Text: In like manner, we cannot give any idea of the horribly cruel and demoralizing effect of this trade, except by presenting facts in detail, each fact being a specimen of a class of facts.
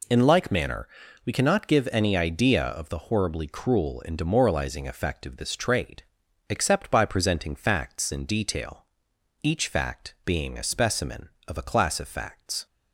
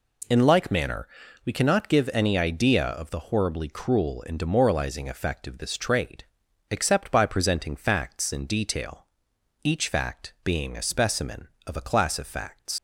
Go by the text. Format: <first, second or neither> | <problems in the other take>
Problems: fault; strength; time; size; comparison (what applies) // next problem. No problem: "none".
first | leaves "facts" unfinished; at 12.7 s; 60 ms